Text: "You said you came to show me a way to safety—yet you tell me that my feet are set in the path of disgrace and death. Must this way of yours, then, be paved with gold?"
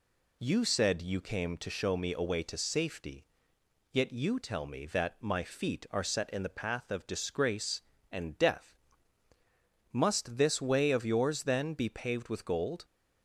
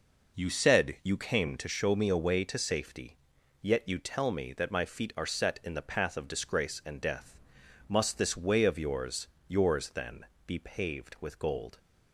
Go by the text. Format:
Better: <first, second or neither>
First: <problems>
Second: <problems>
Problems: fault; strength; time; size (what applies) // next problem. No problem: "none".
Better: first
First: none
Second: says "yours" twice; at 9.4 s